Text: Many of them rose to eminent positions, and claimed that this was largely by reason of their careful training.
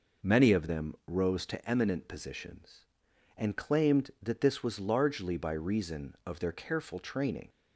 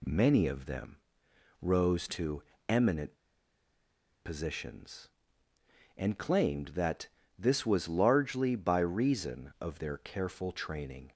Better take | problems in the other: first | pauses between "them" and "rose"; noticeable; at 0.9 s; 0.64 s long // pauses between "to" and "eminent"; slight; at 2.4 s; 0.24 s long // pauses between "eminent" and "positions"; at 3.1 s; 1.0 s long // pauses between "that" and "this"; slight; at 7.0 s; 0.28 s long

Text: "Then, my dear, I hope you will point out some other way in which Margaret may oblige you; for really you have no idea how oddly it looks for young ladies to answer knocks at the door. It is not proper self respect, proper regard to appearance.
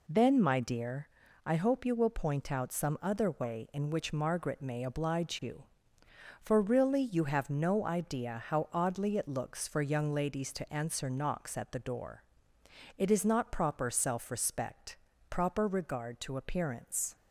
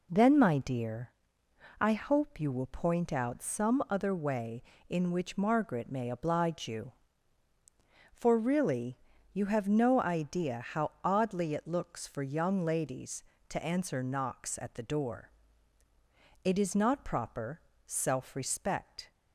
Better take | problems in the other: first | pauses between "really" and "you"; slight; at 8.9 s; 0.36 s long // pauses between "proper" and "self"; slight; at 17.6 s; 0.24 s long // stops before "proper regard to appearance"; at 19.1 s

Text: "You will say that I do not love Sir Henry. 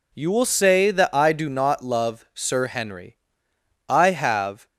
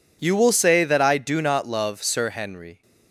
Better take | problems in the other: second | goes on to say "I have"; noticeable; from 3.8 s on; 0.78 s long

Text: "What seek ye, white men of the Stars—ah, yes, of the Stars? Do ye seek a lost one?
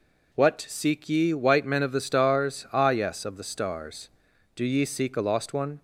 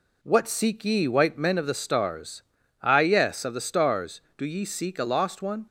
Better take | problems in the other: neither | none

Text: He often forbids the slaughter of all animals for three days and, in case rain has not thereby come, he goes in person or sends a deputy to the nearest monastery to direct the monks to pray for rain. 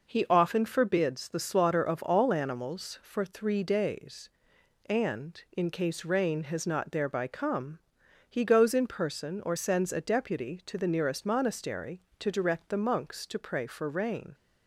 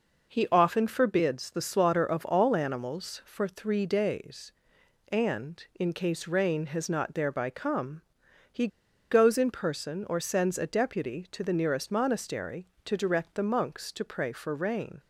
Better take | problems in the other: first | pauses between "he" and "goes"; at 8.6 s; 0.44 s long

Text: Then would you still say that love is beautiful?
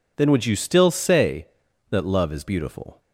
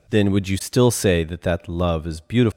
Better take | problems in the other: first | says "that" twice; at 1.4 s

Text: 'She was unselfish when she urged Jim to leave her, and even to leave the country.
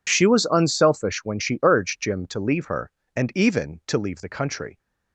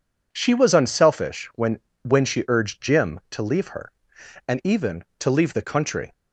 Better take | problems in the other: first | says "when" twice; at 2.0 s

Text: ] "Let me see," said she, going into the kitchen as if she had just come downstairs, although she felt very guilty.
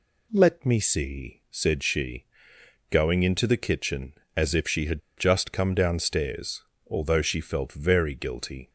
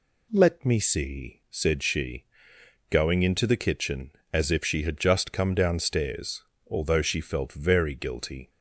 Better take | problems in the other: second | pauses between "had" and "just"; slight; at 5.0 s; 0.16 s long

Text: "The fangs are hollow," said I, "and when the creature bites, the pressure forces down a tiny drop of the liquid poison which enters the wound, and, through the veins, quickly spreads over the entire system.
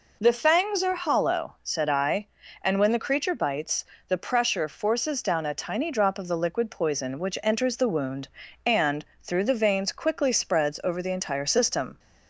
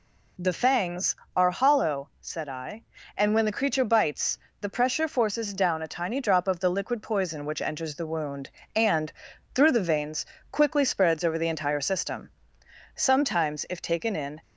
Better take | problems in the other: first | goes on to say "Sometimes if taken in"; from 12.9 s on; 1.4 s long

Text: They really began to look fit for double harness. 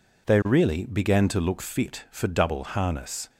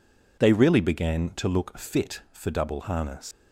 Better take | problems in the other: first | leaves "harness" unfinished; at 3.3 s; 80 ms

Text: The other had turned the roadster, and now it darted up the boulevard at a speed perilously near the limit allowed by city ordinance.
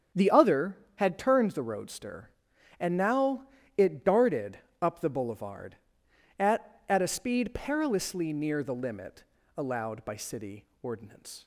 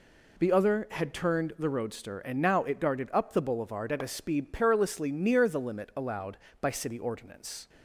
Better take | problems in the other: second | starts louder than the rest; strong; until 1.3 s; 7.5 dB // pauses between "now" and "it"; slight; at 3.4 s; 0.32 s long // pauses between "darted" and "up"; slight; at 4.5 s; 0.22 s long // says "at" twice; at 6.8 s // pauses between "limit" and "allowed"; slight; at 9.2 s; 0.34 s long // pauses between "city" and "ordinance"; slight; at 10.6 s; 0.18 s long

